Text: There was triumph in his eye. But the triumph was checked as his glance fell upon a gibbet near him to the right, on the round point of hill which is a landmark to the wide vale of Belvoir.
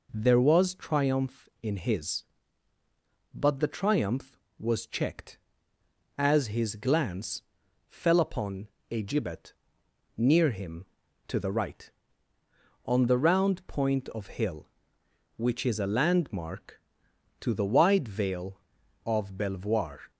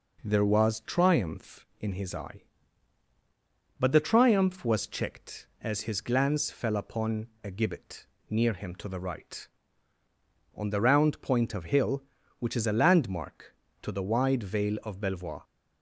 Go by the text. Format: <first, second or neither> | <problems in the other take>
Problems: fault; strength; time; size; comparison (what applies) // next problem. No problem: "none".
second | skips "eye"; at 2.7 s // pauses between "glance" and "fell"; noticeable; at 7.4 s; 0.46 s long // pauses between "upon" and "a"; slight; at 8.6 s; 0.24 s long // pauses between "gibbet" and "near"; noticeable; at 9.5 s; 0.64 s long; slight in the second